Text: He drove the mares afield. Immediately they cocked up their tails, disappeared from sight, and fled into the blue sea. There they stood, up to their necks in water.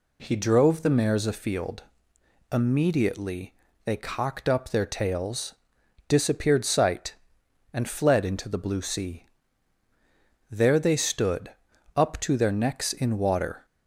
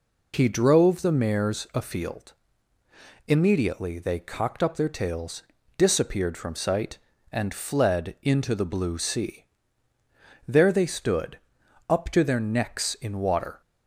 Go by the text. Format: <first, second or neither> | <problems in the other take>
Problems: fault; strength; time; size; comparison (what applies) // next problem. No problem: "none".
second | pauses between "Immediately" and "they"; slight; at 3.5 s; 0.30 s long // skips "from"; at 6.6 s